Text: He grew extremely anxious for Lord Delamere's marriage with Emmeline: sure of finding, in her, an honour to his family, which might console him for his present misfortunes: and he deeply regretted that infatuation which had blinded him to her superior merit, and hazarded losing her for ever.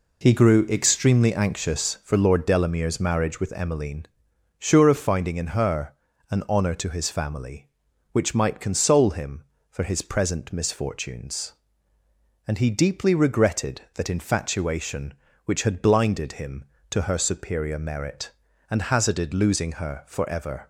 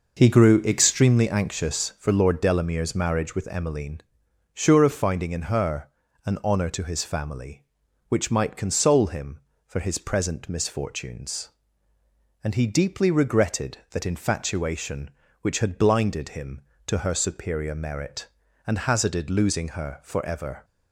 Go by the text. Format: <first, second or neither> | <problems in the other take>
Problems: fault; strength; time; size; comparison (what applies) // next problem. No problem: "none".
first | starts louder than the rest; noticeable; until 1.2 s; 5.5 dB